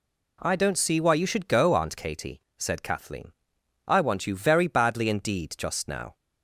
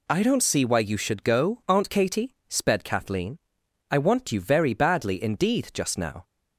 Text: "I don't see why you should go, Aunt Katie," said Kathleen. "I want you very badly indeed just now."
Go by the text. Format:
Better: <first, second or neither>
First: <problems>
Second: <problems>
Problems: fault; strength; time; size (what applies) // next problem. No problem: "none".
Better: first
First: none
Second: says "sped" for "said"; at 2.4 s